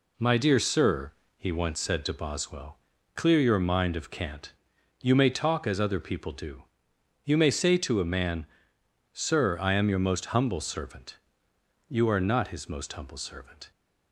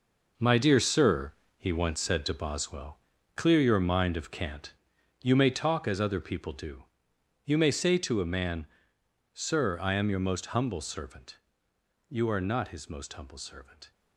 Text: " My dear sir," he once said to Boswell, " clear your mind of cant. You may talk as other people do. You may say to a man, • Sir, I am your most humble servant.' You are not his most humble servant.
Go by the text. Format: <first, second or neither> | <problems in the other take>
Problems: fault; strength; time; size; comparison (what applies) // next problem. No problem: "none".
first | gets quieter; strong; throughout; 8 dB